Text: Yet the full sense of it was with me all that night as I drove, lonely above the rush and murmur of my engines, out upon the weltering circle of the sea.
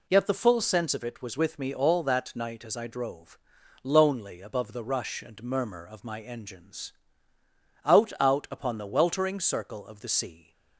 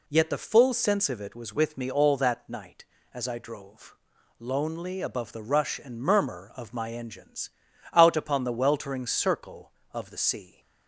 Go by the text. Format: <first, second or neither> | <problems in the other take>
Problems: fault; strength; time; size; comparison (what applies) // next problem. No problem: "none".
second | says "out" twice; at 8.1 s